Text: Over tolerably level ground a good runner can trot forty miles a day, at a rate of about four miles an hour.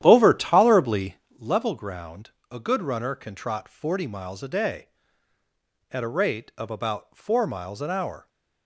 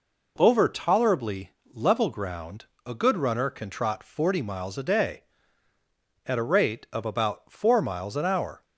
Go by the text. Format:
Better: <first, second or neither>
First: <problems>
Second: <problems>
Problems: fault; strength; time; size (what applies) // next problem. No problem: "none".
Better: second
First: starts louder than the rest; strong; until 1.4 s; 11 dB // pauses between "tolerably" and "level"; slight; at 1.1 s; 0.20 s long // pauses between "ground" and "a"; slight; at 2.2 s; 0.20 s long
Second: pauses between "tolerably" and "level"; slight; at 1.5 s; 0.20 s long // pauses between "ground" and "a"; slight; at 2.6 s; 0.20 s long